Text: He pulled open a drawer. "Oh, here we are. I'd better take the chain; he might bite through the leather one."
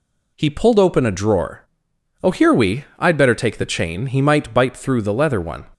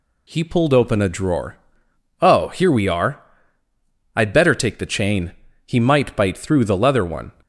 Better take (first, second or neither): second